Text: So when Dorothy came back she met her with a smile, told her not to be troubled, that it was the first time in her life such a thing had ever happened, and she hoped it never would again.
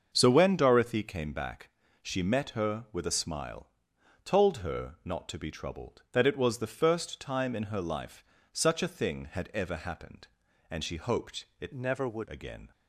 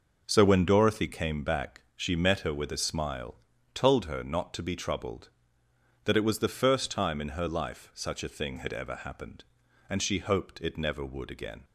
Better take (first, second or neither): second